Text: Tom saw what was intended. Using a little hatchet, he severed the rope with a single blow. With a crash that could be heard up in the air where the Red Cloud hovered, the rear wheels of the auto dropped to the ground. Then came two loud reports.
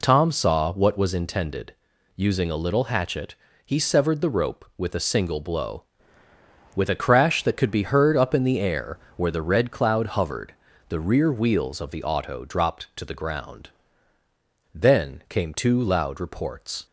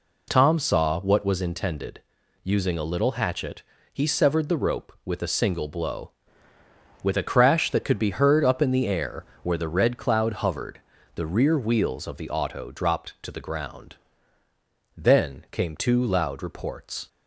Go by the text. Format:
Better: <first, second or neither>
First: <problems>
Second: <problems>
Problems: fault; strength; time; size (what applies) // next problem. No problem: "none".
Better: neither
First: pauses between "air" and "where"; slight; at 8.9 s; 0.18 s long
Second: pauses between "air" and "where"; slight; at 9.2 s; 0.18 s long